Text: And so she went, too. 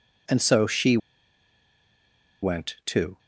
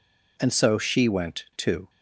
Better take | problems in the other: second | pauses between "she" and "went"; strong; at 0.9 s; 1.4 s long

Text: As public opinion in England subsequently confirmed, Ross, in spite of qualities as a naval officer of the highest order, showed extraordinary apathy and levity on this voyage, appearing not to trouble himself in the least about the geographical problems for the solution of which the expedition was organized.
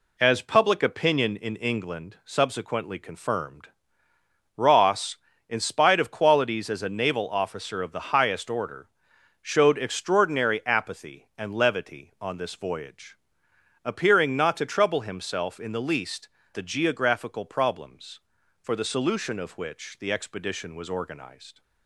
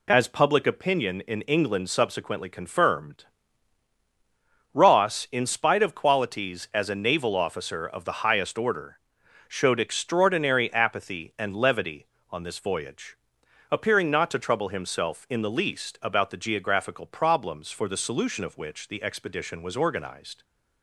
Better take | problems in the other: second | skips "about"; at 16.4 s

